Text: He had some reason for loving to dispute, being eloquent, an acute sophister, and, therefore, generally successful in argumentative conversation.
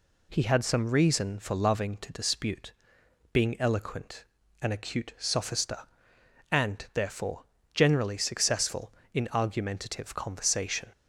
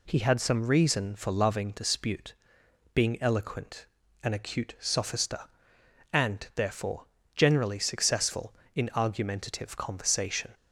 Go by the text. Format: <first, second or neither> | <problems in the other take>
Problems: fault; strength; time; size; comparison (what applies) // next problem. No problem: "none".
first | skips "to"; at 1.7 s